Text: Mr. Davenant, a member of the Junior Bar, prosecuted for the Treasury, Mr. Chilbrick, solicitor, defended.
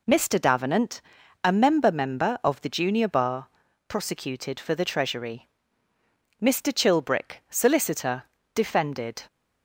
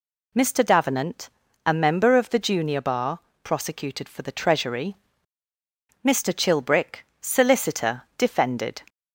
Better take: second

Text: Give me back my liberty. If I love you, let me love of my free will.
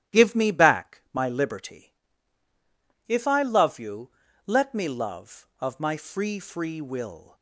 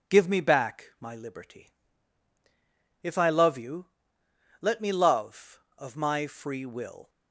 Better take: second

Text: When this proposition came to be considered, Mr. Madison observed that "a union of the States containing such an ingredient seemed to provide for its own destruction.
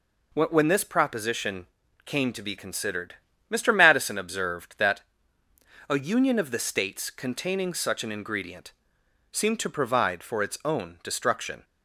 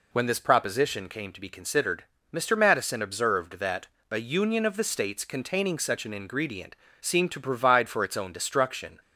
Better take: second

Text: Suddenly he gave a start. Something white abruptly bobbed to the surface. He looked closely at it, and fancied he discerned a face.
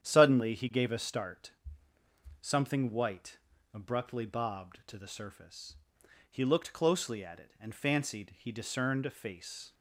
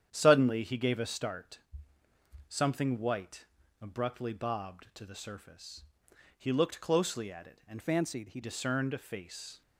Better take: first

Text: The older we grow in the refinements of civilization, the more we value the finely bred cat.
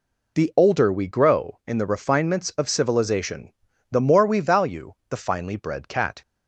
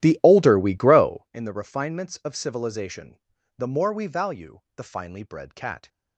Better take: first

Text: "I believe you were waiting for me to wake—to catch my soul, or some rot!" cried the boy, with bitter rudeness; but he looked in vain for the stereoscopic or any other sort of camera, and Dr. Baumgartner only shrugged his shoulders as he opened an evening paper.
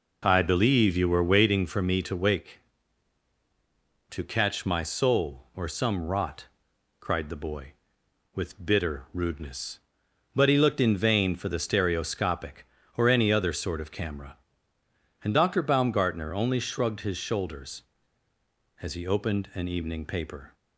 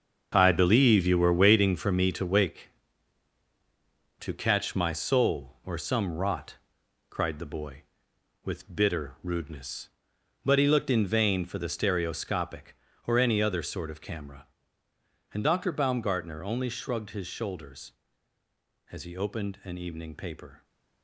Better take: first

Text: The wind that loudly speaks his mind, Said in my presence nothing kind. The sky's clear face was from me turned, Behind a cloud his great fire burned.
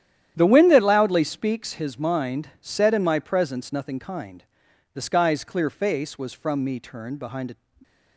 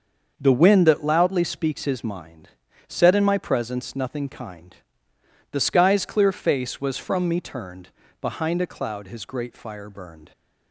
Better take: second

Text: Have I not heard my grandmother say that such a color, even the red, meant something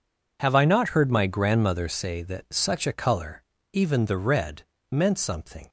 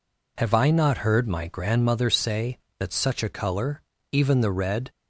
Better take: first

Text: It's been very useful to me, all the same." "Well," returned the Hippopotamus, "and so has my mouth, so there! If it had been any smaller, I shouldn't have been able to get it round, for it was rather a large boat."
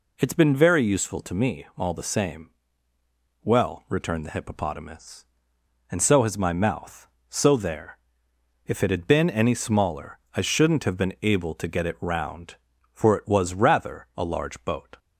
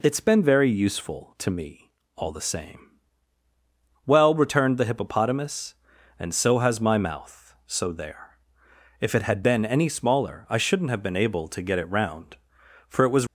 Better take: first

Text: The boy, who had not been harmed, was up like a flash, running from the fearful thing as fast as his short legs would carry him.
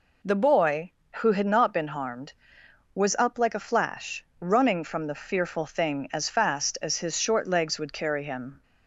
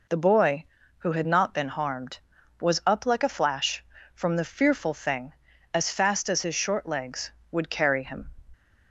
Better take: first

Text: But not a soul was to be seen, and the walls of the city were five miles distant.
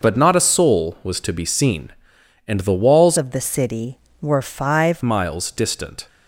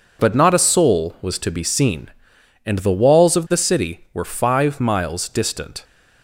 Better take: second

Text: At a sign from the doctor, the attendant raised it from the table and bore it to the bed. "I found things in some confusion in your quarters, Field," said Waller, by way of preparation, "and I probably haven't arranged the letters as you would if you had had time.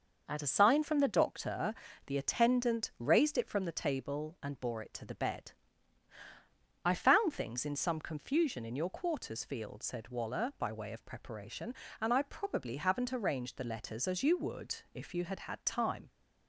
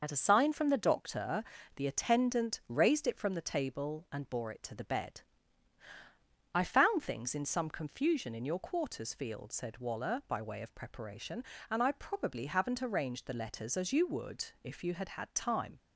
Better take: first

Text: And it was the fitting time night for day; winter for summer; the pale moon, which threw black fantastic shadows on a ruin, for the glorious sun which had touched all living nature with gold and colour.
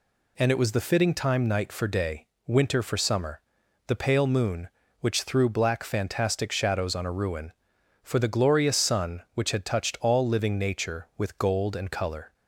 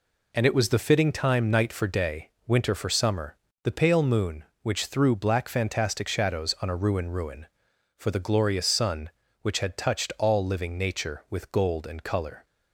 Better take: first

